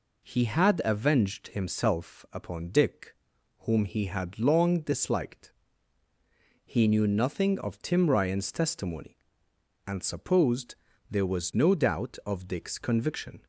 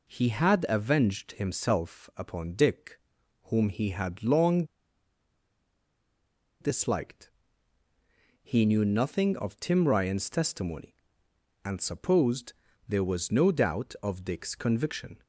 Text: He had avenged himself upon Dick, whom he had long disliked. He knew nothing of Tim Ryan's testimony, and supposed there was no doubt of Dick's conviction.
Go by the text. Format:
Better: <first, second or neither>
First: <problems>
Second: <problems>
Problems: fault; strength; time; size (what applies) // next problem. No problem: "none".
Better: first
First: pauses between "supposed" and "there"; slight; at 10.7 s; 0.34 s long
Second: pauses between "long" and "disliked"; strong; at 4.6 s; 1.9 s long // pauses between "supposed" and "there"; slight; at 12.5 s; 0.34 s long